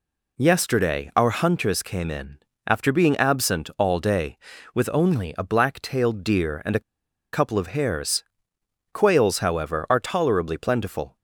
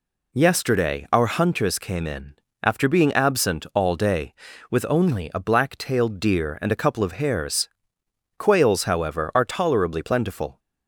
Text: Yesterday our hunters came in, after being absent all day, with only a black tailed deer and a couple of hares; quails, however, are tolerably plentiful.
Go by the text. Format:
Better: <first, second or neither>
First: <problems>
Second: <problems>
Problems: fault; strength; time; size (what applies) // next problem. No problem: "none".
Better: second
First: pauses between "a" and "couple"; noticeable; at 6.8 s; 0.52 s long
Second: none